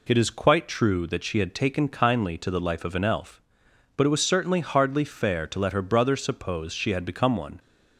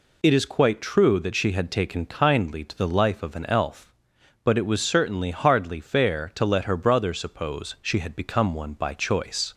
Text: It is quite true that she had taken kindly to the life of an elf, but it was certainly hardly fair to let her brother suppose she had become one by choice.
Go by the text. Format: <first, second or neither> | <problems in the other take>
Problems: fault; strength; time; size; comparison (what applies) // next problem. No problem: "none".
second | stops before "by choice"; at 7.5 s